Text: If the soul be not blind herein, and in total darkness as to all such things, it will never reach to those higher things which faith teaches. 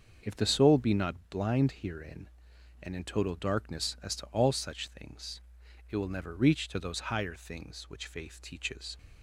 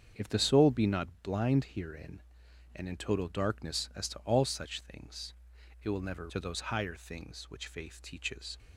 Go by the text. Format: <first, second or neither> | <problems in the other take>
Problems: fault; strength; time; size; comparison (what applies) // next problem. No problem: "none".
first | starts louder than the rest; strong; until 1.3 s; 7.5 dB; also in the first // skips "reach"; at 6.2 s